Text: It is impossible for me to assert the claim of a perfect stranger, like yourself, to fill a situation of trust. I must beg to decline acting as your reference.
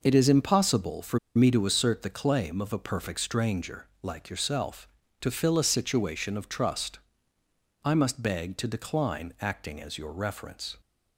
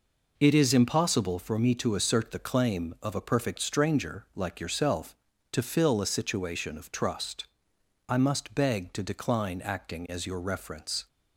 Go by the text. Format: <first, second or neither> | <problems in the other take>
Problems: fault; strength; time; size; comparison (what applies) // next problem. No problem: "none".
second | pauses between "for" and "me"; slight; at 1.1 s; 0.17 s long